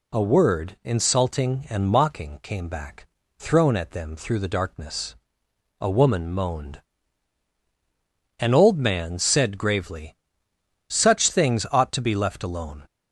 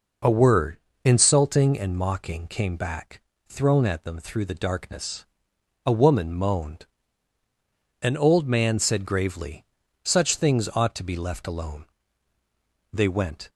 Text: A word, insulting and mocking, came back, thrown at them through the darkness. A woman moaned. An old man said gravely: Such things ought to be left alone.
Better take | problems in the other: first | goes on to say "They went"; from 12.9 s on; 0.56 s long

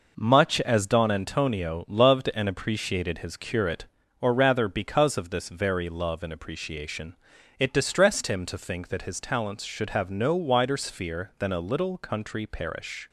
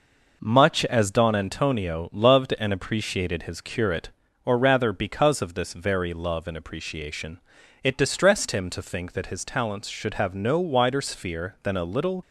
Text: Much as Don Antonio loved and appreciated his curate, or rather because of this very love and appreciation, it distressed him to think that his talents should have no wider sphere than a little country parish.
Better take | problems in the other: first | stops before "country parish"; at 12.2 s

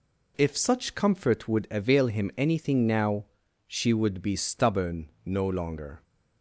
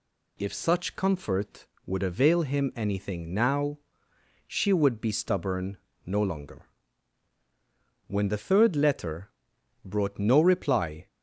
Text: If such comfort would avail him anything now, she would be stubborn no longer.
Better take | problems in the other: first | pauses between "stubborn" and "no"; slight; at 5.7 s; 0.28 s long // goes on to say "When the third letter brought no reply"; strong; from 8.0 s on; 3.0 s long

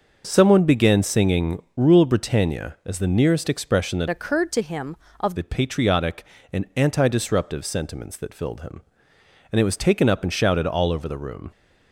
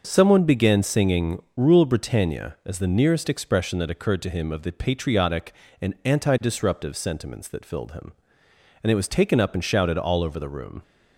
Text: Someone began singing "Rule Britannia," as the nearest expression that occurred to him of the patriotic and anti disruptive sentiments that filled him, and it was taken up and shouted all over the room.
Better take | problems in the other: second | starts louder than the rest; until 1.2 s; 6 dB; noticeable in the second // changes voice from "occurred" to "of"; from 4.0 to 5.3 s; 1.3 s long

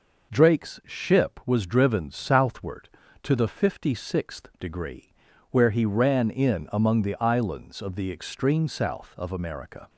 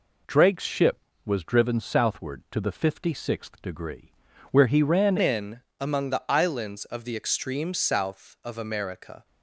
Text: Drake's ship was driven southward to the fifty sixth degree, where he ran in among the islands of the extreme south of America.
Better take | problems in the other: first | changes voice at "in"; from 5.2 s on; 4.0 s long // pauses between "in" and "among"; slight; at 5.6 s; 0.18 s long

